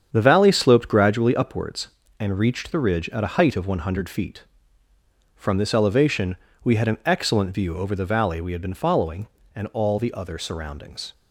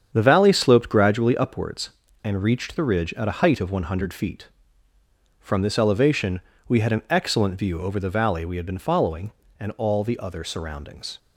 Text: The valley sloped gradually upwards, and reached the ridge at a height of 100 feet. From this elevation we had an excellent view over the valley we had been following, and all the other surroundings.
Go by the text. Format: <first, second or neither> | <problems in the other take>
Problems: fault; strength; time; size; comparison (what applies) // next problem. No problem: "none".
neither | starts louder than the rest; strong; the same in both // pauses between "elevation" and "we"; slight; the same in both